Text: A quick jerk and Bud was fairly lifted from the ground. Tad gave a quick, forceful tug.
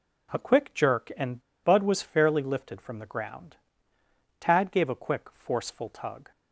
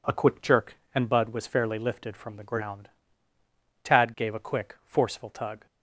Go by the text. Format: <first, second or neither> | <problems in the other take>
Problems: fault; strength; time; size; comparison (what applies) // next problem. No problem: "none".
second | pauses between "and" and "Bud"; slight; at 1.4 s; 0.21 s long